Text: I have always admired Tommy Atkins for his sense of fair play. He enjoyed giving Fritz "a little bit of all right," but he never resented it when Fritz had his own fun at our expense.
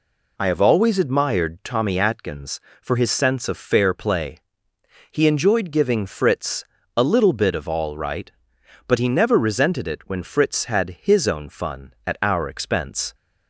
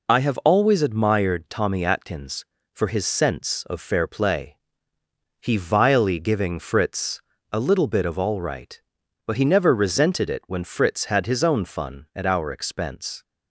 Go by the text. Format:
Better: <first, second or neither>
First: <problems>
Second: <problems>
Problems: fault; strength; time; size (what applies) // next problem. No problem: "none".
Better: first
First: pauses between "Fritz" and "a"; slight; at 6.6 s; 0.32 s long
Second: says "vilely" for "enjoyed"; at 5.5 s // pauses between "Fritz" and "a"; slight; at 7.2 s; 0.32 s long